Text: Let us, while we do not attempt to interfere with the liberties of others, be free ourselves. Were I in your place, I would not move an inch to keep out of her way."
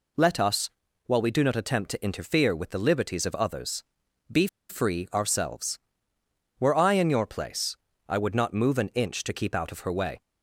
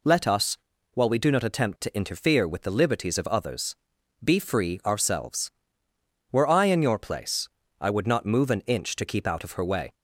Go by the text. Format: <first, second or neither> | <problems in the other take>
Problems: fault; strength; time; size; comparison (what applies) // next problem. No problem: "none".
second | pauses between "be" and "free"; slight; at 4.4 s; 0.22 s long